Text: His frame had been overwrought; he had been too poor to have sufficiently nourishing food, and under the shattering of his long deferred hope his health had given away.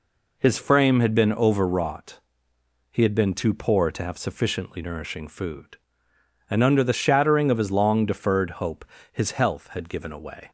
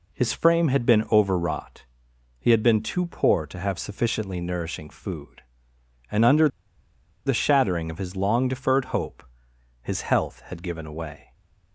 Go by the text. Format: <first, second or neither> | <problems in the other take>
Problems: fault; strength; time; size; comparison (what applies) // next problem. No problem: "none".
first | pauses between "under" and "the"; noticeable; at 6.4 s; 0.78 s long // pauses between "hope" and "his"; noticeable; at 9.2 s; 0.60 s long; slight in the first // stays silent after the last word; slight; from 11.2 s on; 0.5 s long